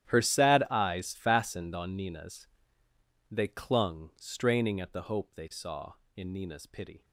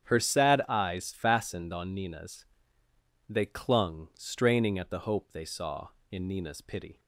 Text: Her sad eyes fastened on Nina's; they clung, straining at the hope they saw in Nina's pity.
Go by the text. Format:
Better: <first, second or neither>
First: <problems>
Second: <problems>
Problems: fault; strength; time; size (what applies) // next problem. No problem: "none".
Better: second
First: gets quieter; strong; throughout; 19 dB // starts louder than the rest; strong; until 1.1 s; 11.5 dB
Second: starts louder than the rest; strong; until 1.1 s; 8.5 dB